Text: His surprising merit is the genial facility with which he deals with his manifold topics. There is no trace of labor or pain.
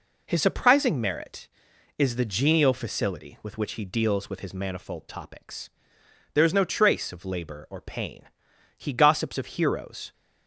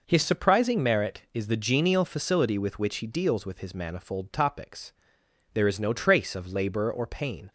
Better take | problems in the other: second | goes on to say "He gossips of heroes"; from 8.7 s on; 1.3 s long

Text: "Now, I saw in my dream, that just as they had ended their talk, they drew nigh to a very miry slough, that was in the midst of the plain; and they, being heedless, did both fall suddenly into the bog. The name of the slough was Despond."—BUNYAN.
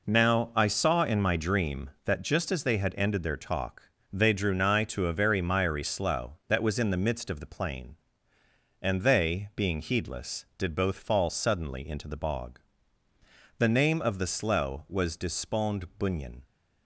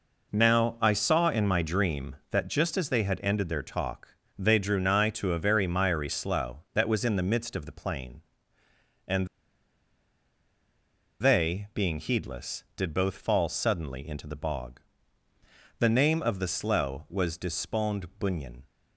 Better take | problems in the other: first | pauses between "and" and "they"; strong; at 9.2 s; 1.9 s long

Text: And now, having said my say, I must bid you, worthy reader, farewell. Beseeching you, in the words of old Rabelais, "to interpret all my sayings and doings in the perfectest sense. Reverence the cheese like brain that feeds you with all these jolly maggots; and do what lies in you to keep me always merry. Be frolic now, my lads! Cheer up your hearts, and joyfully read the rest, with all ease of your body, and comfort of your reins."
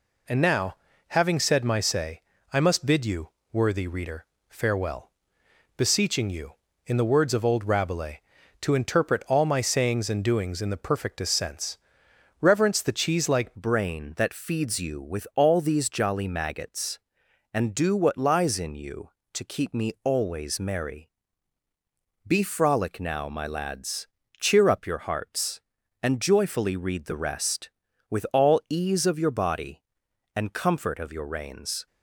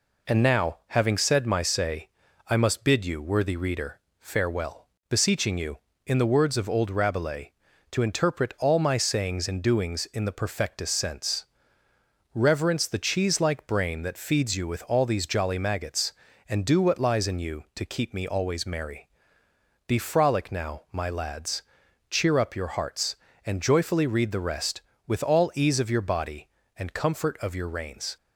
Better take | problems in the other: second | changes voice at "brain"; from 13.5 s on; 18.3 s long

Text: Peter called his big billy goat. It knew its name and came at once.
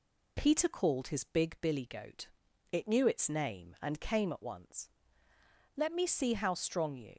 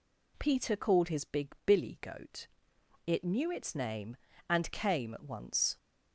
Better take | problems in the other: second | goes on to say "Let me see how strong you"; from 5.7 s on; 1.4 s long

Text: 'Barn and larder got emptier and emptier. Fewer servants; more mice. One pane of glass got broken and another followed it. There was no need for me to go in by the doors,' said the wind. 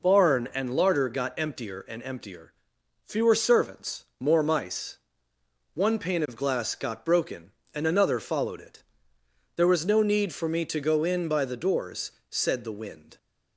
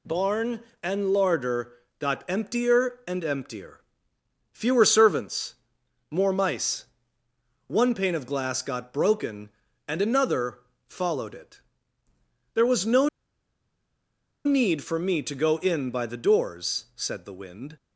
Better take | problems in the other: first | pauses between "larder" and "got"; slight; at 1.7 s; 0.26 s long // pauses between "another" and "followed"; slight; at 10.6 s; 0.28 s long // pauses between "no" and "need"; strong; at 13.0 s; 1.3 s long

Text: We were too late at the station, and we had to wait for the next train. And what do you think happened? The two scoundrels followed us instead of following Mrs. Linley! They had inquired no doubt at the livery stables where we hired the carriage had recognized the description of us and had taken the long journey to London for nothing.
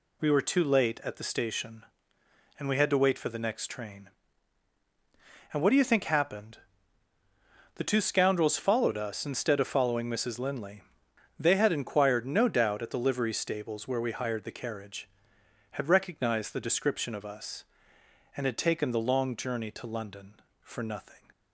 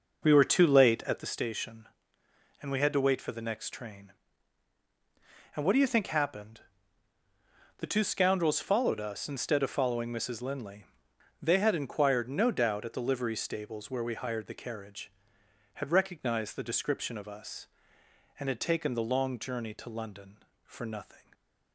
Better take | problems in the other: first | starts louder than the rest; noticeable; until 1.3 s; 5 dB

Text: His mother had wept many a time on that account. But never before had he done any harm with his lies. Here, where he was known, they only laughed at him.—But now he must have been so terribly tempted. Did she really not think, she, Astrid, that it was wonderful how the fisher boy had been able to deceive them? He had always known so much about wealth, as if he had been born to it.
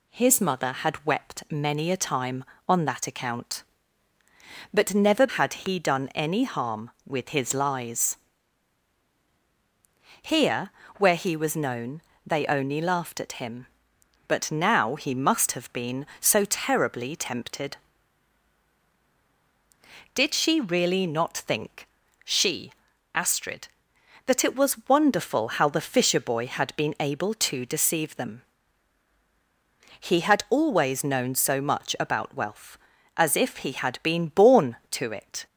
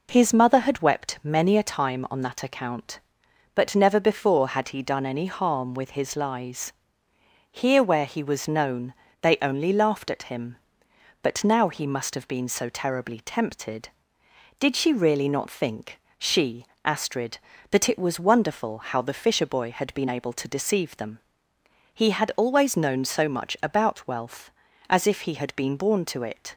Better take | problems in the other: second | skips "before"; at 5.2 s

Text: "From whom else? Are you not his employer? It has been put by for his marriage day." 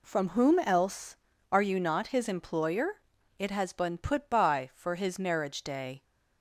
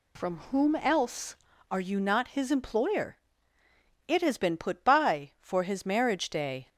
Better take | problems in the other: neither | none

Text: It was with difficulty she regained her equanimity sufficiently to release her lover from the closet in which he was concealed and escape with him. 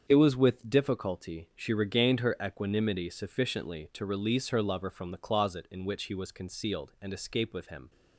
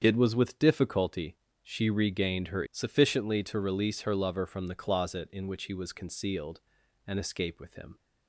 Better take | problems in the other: first | starts louder than the rest; strong; until 1.0 s; 7.5 dB; strong in the first // pauses between "difficulty" and "she"; slight; at 1.3 s; 0.26 s long // skips "equanimity"; at 2.6 s

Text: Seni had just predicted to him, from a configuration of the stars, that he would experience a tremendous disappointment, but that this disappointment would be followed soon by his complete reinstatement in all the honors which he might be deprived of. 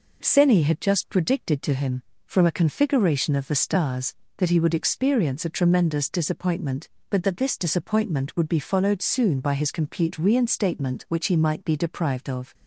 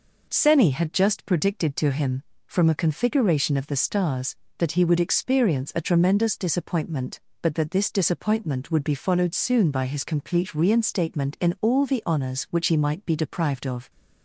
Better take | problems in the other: second | skips "in all the honors"; at 11.0 s

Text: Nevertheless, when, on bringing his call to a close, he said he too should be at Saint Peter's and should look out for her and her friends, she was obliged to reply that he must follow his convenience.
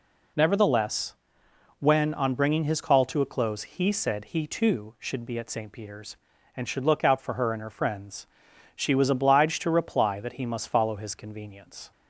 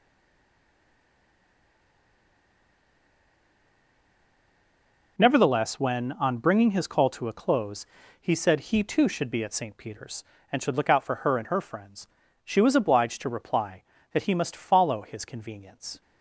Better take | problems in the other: first | stays silent before the first word; strong; until 5.1 s; 5.1 s long

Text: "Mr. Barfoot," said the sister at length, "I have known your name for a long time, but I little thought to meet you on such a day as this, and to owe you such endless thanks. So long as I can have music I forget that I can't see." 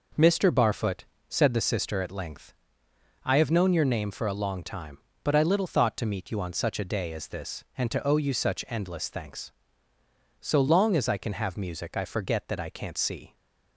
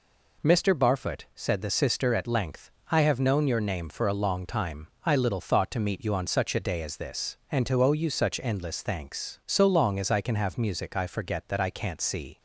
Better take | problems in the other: first | skips "but"; at 4.9 s

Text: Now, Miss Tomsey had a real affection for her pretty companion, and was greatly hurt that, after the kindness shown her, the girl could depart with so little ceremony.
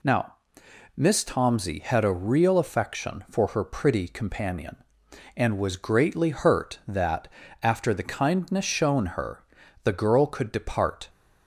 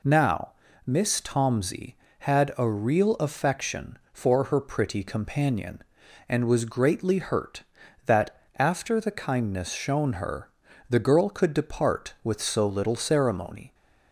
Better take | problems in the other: second | stops before "with so little ceremony"; at 11.0 s

